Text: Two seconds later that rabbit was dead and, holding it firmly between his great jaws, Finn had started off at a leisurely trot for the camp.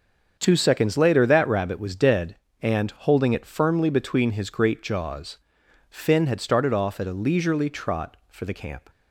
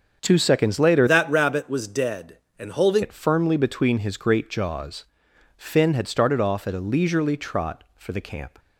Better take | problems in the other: first | starts louder than the rest; strong; until 1.2 s; 7.5 dB; also in the first // changes voice from "that" to "holding"; from 1.0 to 3.0 s; 2.0 s long

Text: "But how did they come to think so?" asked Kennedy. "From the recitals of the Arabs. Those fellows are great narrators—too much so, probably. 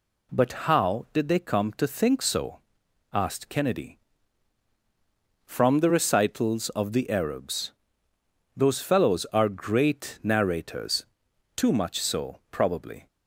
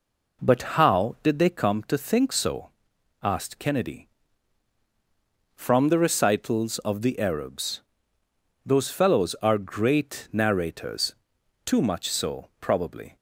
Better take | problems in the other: first | starts louder than the rest; noticeable; until 1.7 s; 4.5 dB

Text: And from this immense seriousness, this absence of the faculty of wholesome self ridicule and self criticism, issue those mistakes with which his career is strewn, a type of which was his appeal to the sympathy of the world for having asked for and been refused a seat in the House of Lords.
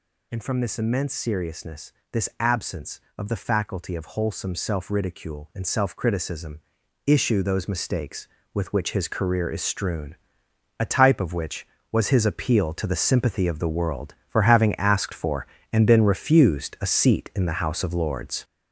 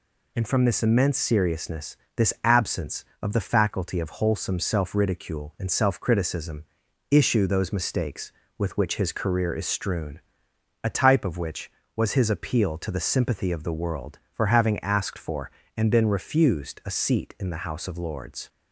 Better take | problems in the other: second | gets louder; throughout; 7 dB

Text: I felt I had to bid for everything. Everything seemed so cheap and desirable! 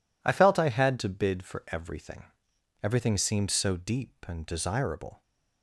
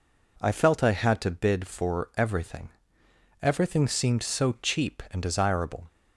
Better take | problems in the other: second | says "deep" for "cheap"; at 3.7 s

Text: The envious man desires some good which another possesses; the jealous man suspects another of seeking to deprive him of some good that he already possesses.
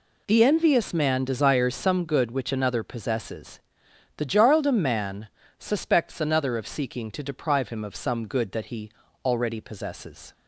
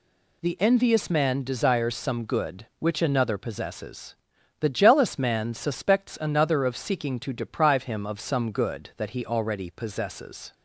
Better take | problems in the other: second | says "jarldom" for "jealous"; at 4.2 s // pauses between "man" and "suspects"; slight; at 5.2 s; 0.32 s long // pauses between "he" and "already"; slight; at 8.8 s; 0.36 s long

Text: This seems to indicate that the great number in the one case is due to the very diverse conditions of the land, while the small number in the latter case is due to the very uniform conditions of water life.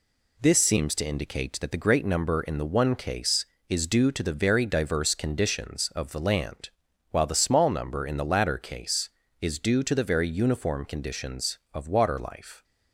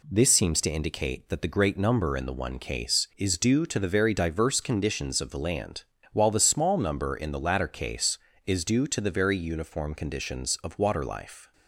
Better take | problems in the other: neither | none

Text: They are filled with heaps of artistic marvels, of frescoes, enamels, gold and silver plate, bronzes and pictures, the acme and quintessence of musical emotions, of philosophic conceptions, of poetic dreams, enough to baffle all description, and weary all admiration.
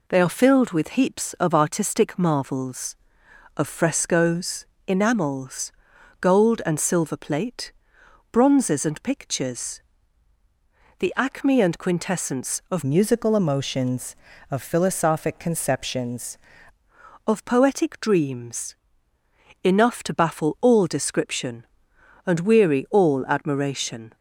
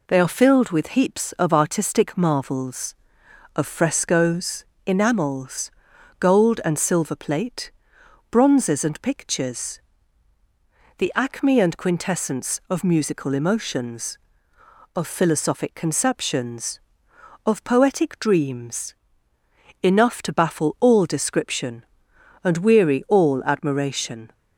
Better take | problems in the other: second | changes voice from "musical" to "conceptions"; from 12.8 to 16.3 s; 3.5 s long

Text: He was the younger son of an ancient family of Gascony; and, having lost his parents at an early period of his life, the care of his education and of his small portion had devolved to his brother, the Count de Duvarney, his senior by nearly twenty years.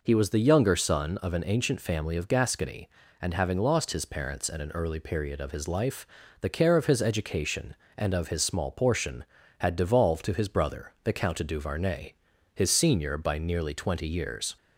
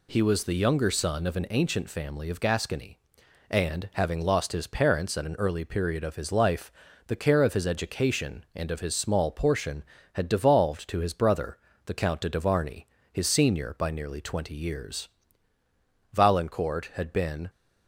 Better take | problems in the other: first | goes on to say "Valancourt had been"; from 16.1 s on; 1.3 s long

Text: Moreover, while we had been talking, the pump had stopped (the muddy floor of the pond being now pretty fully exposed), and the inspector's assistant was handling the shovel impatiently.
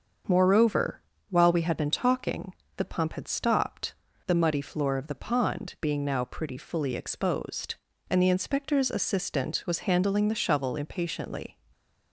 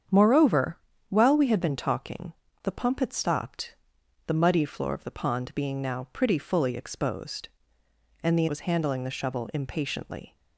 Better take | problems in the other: first | starts louder than the rest; strong; until 1.4 s; 8 dB; also in the first // skips "inspector's assistant"; at 8.4 s

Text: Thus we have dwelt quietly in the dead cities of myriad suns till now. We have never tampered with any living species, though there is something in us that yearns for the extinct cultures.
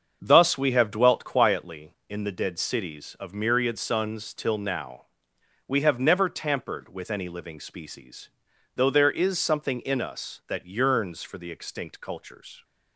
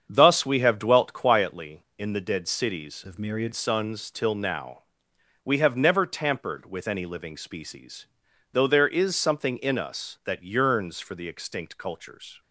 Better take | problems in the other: first | starts louder than the rest; strong; until 1.1 s; 7.5 dB; also in the first // changes voice from "of" to "myriad"; from 3.0 to 3.5 s; 0.5 s long

